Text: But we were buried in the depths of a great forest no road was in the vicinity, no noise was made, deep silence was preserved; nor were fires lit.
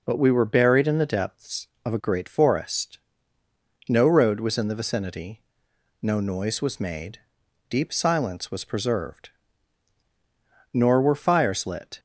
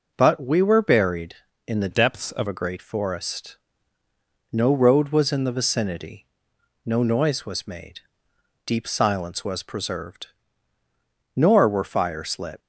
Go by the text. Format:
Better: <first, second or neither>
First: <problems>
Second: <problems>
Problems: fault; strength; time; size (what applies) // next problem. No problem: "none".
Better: first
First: pauses between "forest" and "no"; noticeable; at 2.9 s; 0.92 s long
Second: changes voice from "depths" to "of"; from 1.9 to 2.4 s; 0.5 s long // pauses between "forest" and "no"; noticeable; at 3.5 s; 0.94 s long